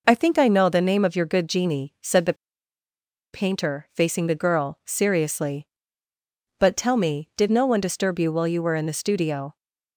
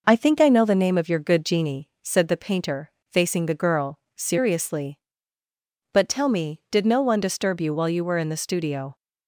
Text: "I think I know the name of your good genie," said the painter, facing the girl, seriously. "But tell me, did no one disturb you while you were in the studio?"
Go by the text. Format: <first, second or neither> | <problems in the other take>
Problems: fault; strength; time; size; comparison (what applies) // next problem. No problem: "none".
second | pauses between "the" and "painter"; at 2.3 s; 0.99 s long